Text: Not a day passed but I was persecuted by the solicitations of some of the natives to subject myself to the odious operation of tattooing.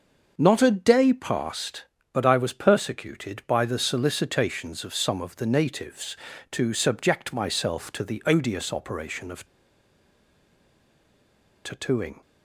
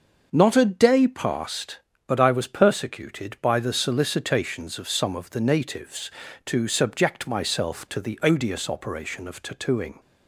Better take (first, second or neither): second